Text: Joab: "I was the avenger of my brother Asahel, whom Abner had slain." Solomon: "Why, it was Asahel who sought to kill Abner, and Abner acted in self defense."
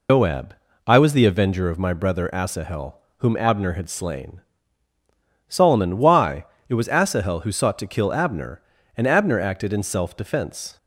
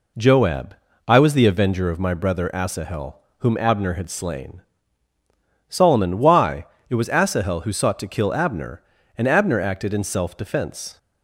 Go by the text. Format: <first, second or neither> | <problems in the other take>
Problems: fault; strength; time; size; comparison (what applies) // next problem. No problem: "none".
second | loses the start of "Joab"; at 0.0 s; 145 ms